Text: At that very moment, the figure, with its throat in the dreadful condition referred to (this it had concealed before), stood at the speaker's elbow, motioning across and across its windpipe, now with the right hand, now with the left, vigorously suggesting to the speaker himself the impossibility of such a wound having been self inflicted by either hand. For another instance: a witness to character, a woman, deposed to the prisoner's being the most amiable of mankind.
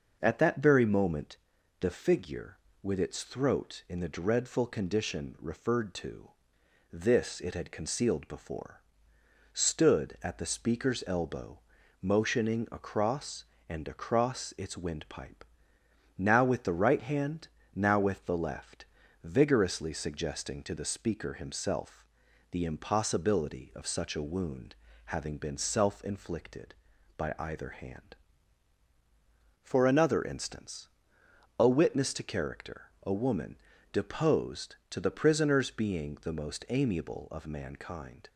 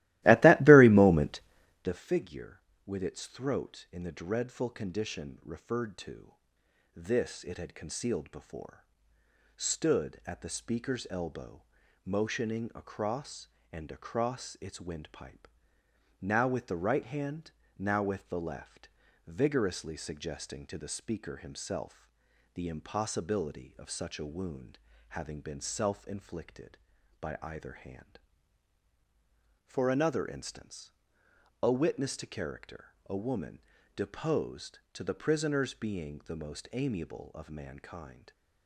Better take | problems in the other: first | starts louder than the rest; strong; until 1.9 s; 17.5 dB // pauses between "himself" and "the"; noticeable; at 22.0 s; 0.48 s long; noticeable in the first // pauses between "wound" and "having"; slight; at 24.7 s; 0.30 s long; slight in the first

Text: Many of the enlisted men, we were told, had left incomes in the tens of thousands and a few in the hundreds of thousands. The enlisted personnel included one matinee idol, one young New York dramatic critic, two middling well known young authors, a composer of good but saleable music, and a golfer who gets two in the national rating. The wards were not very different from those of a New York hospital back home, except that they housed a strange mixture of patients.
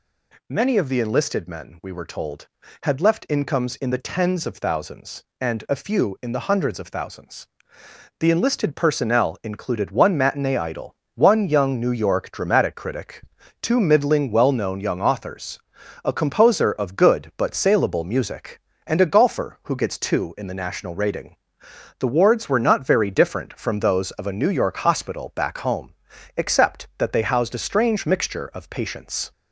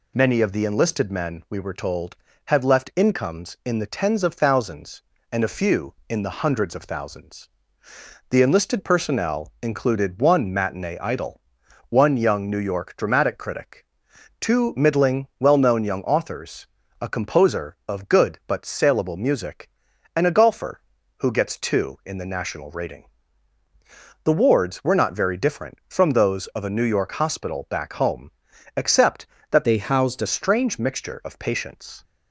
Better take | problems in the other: first | changes voice from "they" to "a"; from 29.6 to 30.2 s; 0.6 s long

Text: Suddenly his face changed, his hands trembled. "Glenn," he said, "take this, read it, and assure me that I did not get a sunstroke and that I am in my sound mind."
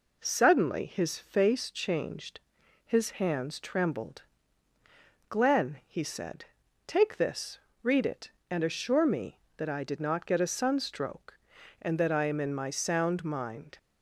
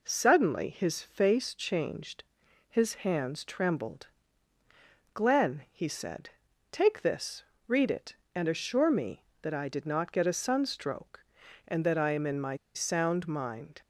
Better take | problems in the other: first | pauses between "my" and "sound"; slight; at 12.5 s; 0.17 s long

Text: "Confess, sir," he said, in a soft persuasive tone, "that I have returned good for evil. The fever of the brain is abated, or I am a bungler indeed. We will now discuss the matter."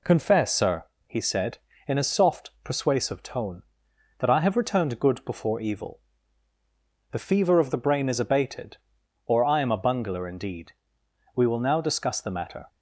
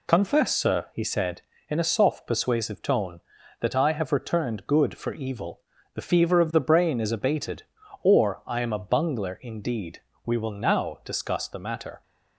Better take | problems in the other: second | says "before" for "for"; at 5.2 s

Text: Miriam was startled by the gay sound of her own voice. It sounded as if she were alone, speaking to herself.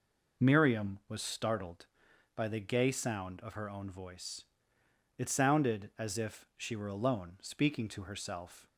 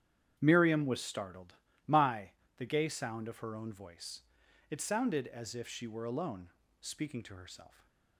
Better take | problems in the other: first | starts louder than the rest; strong; until 1.3 s; 9.5 dB // says "my" for "by"; at 1.8 s

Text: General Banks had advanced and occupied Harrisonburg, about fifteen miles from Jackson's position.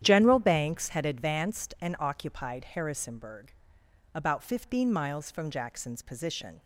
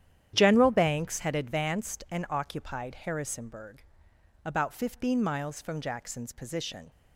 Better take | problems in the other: neither | starts louder than the rest; strong; the same in both

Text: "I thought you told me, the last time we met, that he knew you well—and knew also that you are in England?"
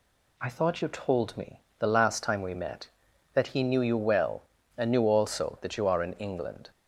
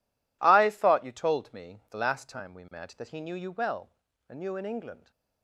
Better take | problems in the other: first | skips "also that you are"; at 4.5 s

